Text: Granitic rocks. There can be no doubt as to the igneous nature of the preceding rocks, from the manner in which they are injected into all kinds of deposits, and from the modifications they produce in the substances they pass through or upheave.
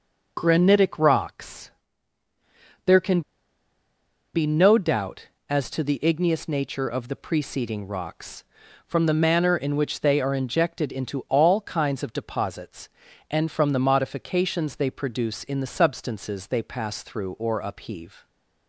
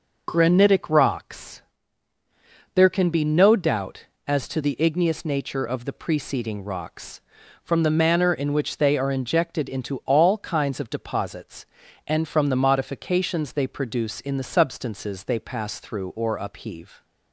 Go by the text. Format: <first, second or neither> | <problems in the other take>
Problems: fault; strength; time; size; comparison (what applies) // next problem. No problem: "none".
second | pauses between "can" and "be"; at 3.2 s; 1.1 s long